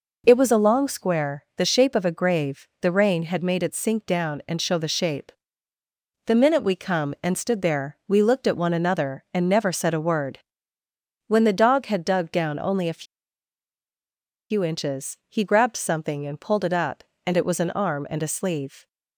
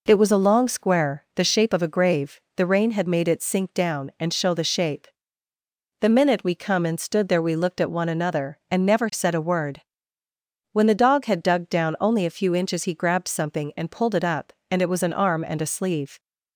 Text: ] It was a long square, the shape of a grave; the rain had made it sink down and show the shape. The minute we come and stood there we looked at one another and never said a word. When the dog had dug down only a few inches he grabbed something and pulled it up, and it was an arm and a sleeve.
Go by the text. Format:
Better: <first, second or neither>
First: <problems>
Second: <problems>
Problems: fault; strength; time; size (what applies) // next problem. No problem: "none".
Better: second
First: pauses between "a" and "few"; strong; at 13.0 s; 1.4 s long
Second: none